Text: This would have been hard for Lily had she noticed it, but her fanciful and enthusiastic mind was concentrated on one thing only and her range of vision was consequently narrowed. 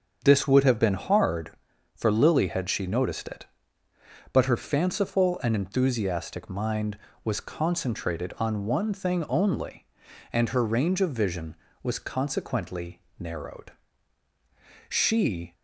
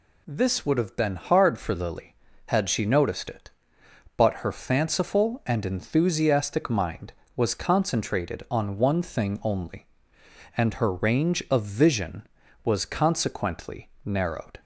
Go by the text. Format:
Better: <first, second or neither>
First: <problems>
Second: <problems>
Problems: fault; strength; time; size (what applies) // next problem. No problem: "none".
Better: second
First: starts louder than the rest; strong; until 1.2 s; 7 dB // pauses between "consequently" and "narrowed"; slight; at 12.9 s; 0.18 s long // goes on to say "She"; noticeable; from 14.8 s on; 0.66 s long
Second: pauses between "consequently" and "narrowed"; slight; at 13.8 s; 0.16 s long